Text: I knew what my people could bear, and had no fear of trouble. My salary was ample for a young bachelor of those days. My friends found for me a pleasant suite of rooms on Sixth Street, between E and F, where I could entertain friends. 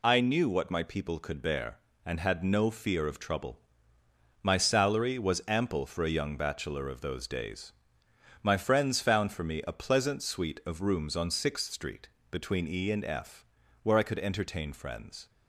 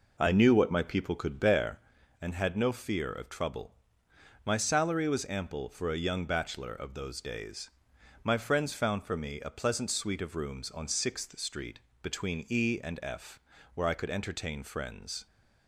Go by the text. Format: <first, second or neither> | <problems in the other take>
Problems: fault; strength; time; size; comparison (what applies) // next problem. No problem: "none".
first | starts louder than the rest; noticeable; until 1.9 s; 4.5 dB